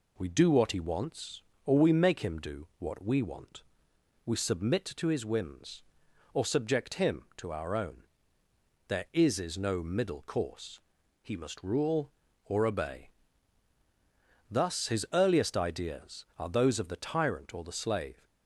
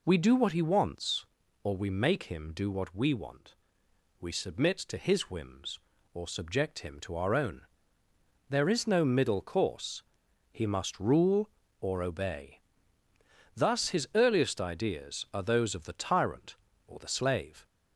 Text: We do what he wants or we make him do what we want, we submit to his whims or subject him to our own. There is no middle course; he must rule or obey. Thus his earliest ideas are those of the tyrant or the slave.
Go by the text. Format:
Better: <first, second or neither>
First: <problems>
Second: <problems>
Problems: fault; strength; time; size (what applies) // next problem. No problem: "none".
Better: second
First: says "is" twice; at 9.3 s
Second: none